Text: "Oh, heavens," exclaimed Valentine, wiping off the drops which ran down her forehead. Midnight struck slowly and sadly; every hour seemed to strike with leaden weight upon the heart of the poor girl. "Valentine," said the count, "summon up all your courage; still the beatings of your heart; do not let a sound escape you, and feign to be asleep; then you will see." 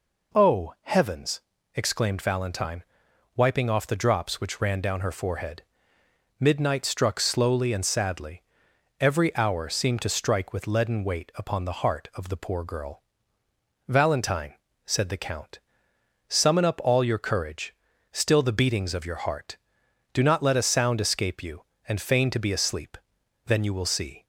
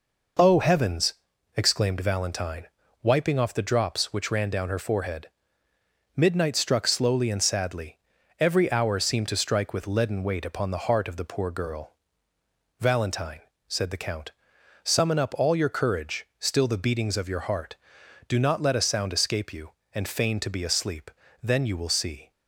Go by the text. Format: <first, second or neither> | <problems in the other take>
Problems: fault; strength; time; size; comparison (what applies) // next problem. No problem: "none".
neither | none